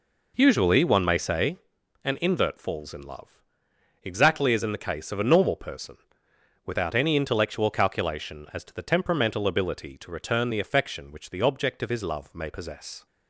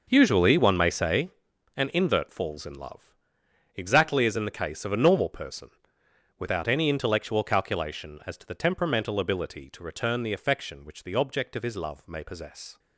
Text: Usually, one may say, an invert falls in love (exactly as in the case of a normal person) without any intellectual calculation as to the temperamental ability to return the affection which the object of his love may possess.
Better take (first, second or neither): first